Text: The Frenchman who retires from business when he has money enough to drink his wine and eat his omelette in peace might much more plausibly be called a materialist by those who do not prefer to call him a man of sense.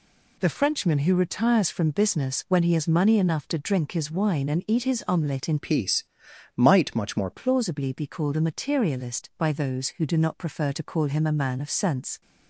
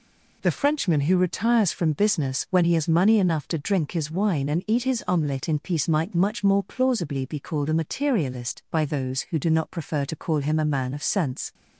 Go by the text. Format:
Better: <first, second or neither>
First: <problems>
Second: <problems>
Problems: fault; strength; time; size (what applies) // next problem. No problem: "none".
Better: second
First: changes voice from "peace" to "more"; from 5.5 to 7.2 s; 1.7 s long // pauses between "peace" and "might"; noticeable; at 6.0 s; 0.52 s long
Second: none